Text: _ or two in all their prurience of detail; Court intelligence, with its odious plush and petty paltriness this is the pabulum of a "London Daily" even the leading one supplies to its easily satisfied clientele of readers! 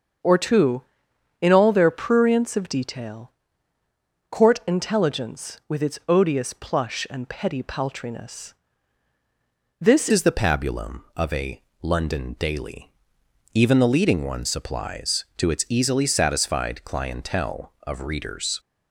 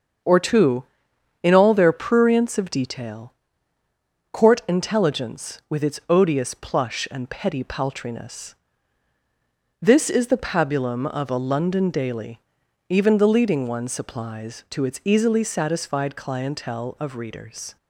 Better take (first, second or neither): second